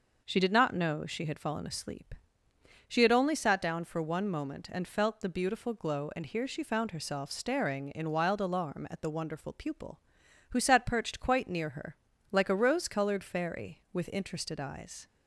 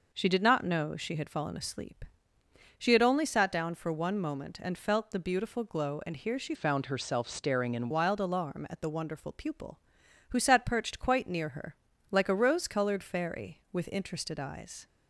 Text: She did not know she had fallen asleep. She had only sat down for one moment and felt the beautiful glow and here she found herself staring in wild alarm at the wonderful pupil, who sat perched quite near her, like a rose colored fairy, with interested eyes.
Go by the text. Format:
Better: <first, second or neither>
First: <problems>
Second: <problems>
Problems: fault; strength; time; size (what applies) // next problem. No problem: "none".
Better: first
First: none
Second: changes voice from "found" to "in"; from 6.5 to 7.8 s; 1.3 s long